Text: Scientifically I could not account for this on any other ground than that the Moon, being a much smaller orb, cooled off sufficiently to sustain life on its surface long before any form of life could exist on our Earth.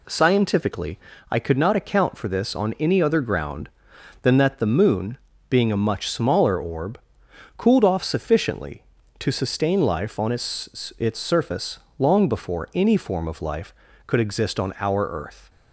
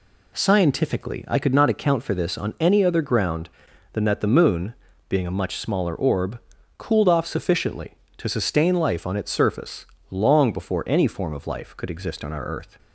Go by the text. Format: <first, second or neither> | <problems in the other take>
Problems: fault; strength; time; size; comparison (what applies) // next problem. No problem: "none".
second | pauses between "Scientifically" and "I"; slight; at 0.9 s; 0.32 s long // says "its" twice; at 10.9 s // pauses between "surface" and "long"; slight; at 11.7 s; 0.20 s long; slight in the second